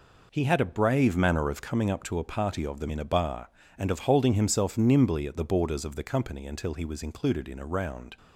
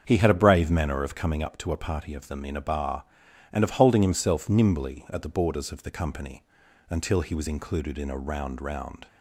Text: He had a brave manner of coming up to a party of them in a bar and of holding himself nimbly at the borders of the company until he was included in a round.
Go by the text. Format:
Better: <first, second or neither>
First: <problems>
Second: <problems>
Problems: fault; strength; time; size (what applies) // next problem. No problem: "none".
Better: first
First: none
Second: starts louder than the rest; strong; until 1.0 s; 7 dB // pauses between "company" and "until"; at 6.4 s; 0.44 s long // says "round" twice; at 8.6 s